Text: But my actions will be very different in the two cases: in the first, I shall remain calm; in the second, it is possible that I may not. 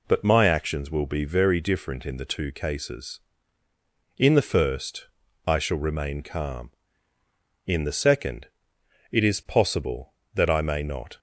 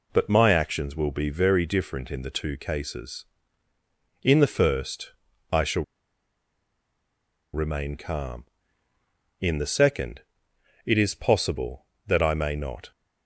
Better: first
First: none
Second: pauses between "shall" and "remain"; strong; at 5.8 s; 1.6 s long

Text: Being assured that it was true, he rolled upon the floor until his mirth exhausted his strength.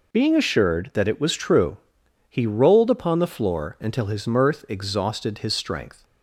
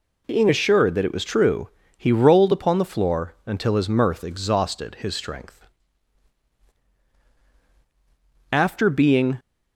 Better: first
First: none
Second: goes on to say "After being"; noticeable; from 8.5 s on; 0.88 s long

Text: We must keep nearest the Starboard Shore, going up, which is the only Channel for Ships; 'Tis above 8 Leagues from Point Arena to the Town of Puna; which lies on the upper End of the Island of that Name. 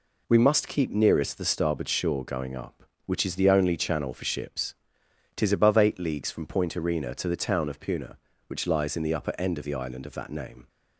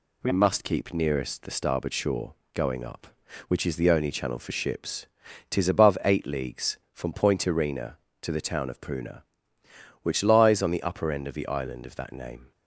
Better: second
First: says "in" for "on"; at 8.9 s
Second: none

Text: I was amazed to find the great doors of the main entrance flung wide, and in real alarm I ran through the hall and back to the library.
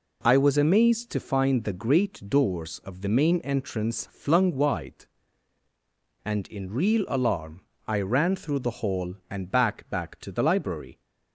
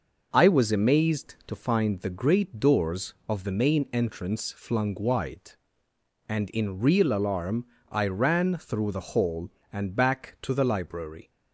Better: second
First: pauses between "alarm" and "I"; slight; at 7.6 s; 0.26 s long // says "back" twice; at 9.8 s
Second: pauses between "alarm" and "I"; slight; at 7.6 s; 0.24 s long

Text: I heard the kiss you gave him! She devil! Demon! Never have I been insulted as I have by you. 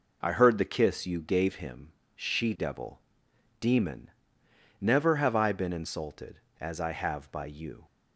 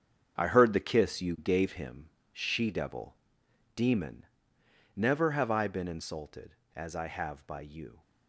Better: first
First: none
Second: gets quieter; strong; throughout; 10.5 dB

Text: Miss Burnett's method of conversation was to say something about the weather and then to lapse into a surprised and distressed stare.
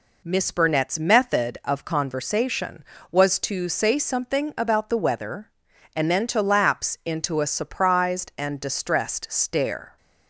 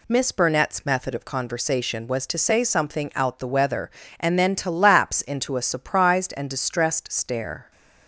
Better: first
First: none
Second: says "out" for "about"; at 3.1 s

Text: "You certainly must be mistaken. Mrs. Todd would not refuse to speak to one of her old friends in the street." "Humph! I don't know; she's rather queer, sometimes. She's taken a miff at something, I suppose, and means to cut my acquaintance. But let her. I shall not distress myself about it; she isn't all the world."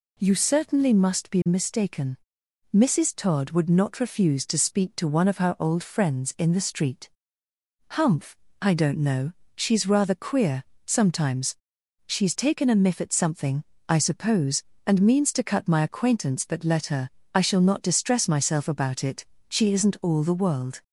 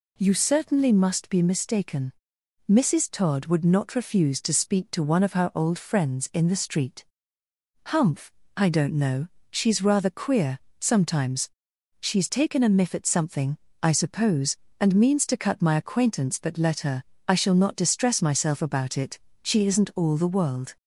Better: neither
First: none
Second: none

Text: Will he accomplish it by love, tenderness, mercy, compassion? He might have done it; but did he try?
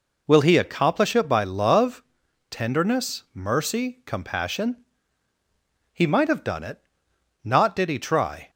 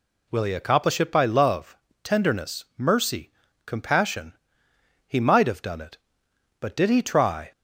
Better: second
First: says "not" for "but"; at 7.4 s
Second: none

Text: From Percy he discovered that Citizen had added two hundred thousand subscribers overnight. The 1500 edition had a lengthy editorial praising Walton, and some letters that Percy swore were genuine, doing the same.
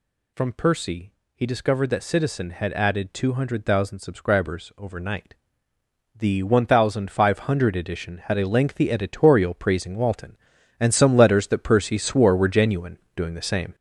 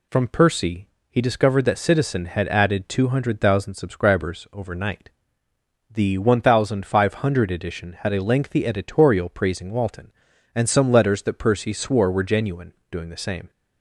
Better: second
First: gets louder; throughout; 6.5 dB // pauses between "Percy" and "he"; slight; at 1.1 s; 0.22 s long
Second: pauses between "Percy" and "he"; slight; at 0.8 s; 0.22 s long

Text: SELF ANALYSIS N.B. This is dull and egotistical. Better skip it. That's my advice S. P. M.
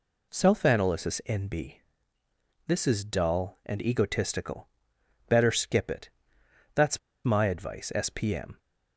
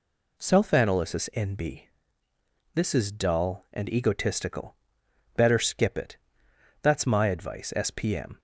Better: second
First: pauses between "That's" and "my"; slight; at 6.9 s; 0.26 s long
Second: none

